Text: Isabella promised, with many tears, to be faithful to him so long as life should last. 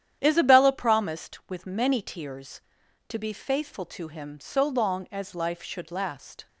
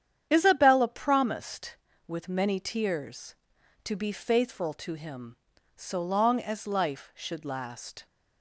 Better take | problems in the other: neither | starts louder than the rest; strong; the same in both

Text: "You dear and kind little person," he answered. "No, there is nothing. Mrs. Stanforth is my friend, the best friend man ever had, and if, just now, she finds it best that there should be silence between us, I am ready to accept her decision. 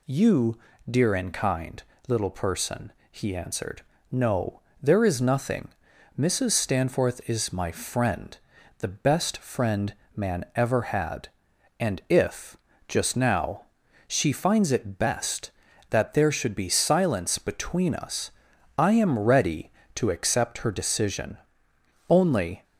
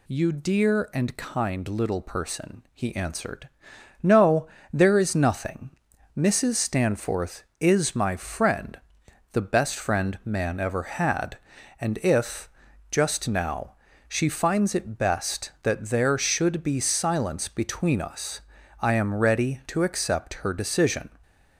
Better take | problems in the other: second | pauses between "You" and "dear"; slight; at 0.5 s; 0.32 s long // pauses between "kind" and "little"; slight; at 1.8 s; 0.28 s long // pauses between "friend" and "man"; slight; at 9.9 s; 0.20 s long // goes on to say "Only"; from 22.0 s on; 0.54 s long

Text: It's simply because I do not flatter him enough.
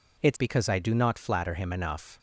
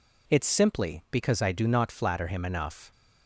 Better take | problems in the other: second | skips "simply"; at 0.3 s

